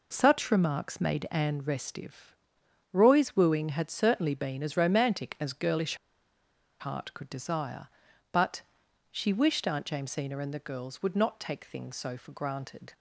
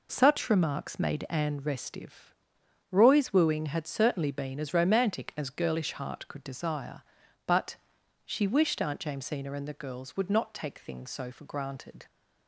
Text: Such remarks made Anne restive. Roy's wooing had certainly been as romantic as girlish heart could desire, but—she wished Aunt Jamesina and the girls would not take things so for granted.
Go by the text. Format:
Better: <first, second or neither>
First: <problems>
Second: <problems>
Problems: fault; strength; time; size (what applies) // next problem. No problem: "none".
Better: second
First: pauses between "girlish" and "heart"; noticeable; at 5.9 s; 0.84 s long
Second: none